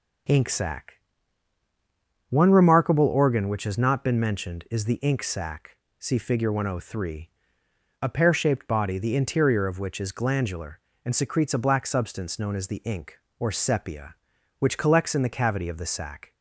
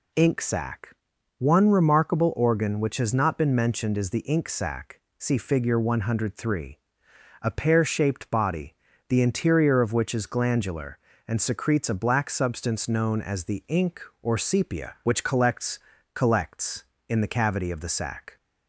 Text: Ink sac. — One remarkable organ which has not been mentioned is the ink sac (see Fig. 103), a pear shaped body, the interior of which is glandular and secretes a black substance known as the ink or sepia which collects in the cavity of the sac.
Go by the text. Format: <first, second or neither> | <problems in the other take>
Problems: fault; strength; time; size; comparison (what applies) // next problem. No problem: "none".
first | says "collects" twice; at 16.1 s